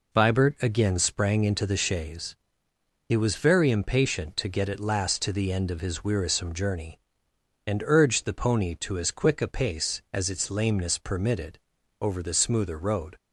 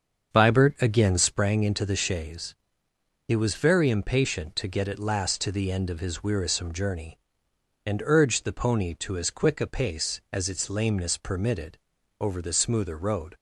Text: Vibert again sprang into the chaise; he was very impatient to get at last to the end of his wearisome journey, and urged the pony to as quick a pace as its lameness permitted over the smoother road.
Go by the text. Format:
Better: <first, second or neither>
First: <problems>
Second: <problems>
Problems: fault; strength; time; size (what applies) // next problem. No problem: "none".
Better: first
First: pauses between "permitted" and "over"; at 11.5 s; 0.44 s long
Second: starts louder than the rest; until 1.5 s; 7 dB // pauses between "permitted" and "over"; at 11.7 s; 0.44 s long